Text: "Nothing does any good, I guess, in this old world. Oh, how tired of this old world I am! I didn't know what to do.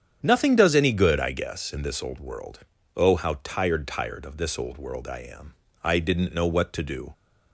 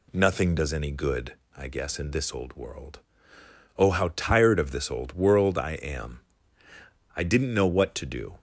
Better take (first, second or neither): second